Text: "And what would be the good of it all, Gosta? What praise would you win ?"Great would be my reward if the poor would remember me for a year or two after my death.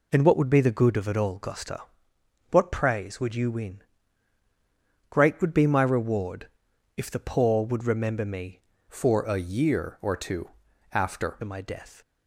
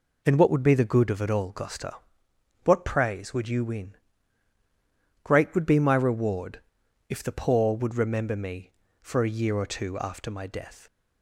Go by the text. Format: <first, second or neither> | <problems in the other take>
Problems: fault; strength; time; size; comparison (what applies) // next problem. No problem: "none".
second | pauses between "reward" and "if"; noticeable; at 6.4 s; 0.48 s long; noticeable in the second // changes voice from "for" to "after"; from 8.8 to 11.3 s; 2.5 s long // pauses between "two" and "after"; at 10.4 s; 0.42 s long